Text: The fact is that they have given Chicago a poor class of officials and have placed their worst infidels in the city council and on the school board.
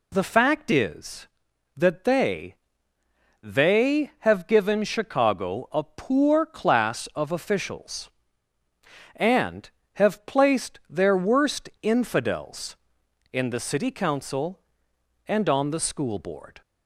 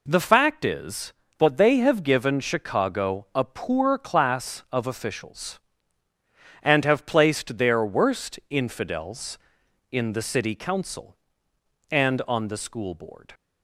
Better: second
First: says "they" twice; at 3.4 s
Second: none

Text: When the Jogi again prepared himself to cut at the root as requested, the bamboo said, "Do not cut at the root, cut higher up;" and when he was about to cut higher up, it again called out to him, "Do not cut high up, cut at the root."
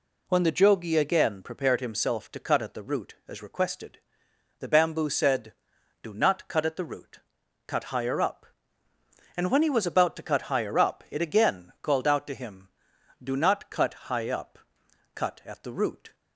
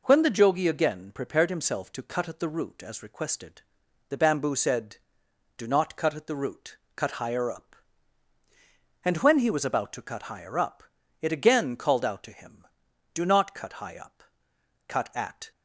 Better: first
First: none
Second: stops before "the root"; at 15.5 s

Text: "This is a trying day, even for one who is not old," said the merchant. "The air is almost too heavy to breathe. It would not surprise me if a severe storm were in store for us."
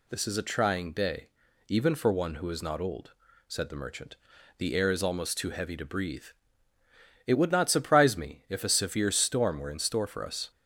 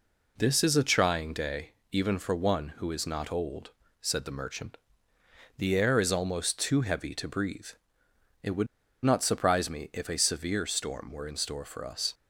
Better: first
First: none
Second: pauses between "would" and "not"; at 8.6 s; 0.37 s long

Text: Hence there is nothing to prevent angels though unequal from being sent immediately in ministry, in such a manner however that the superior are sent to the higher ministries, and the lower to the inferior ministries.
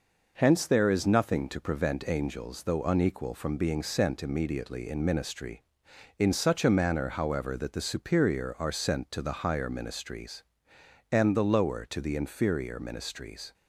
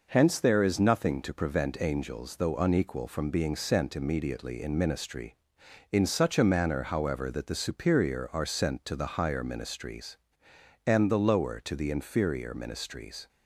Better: neither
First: none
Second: none

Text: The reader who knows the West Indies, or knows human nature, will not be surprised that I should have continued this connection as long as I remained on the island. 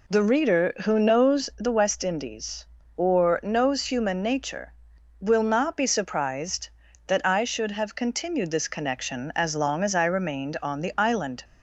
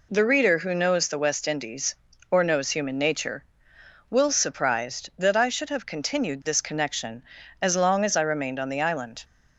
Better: first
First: none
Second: skips "not be"; at 4.3 s

